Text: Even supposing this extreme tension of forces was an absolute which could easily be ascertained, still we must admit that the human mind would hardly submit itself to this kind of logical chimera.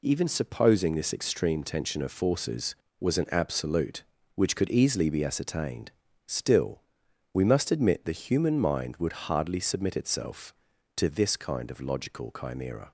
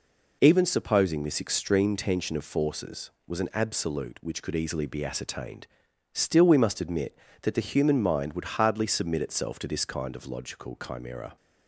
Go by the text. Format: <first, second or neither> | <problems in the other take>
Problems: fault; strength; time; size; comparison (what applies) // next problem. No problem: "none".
second | pauses between "still" and "we"; noticeable; at 6.8 s; 0.52 s long // skips "that"; at 8.0 s